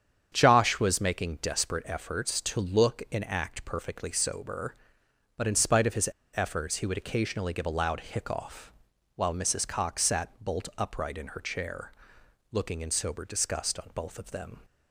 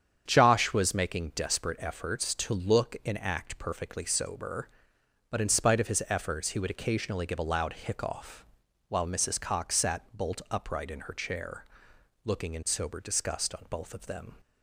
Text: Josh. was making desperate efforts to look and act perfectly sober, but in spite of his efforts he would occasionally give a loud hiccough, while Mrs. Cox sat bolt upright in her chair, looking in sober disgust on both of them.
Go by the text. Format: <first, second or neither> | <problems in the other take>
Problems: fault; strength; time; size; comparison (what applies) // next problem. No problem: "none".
second | starts louder than the rest; strong; until 1.3 s; 8 dB; strong in the second // pauses between "his" and "efforts"; slight; at 6.0 s; 0.26 s long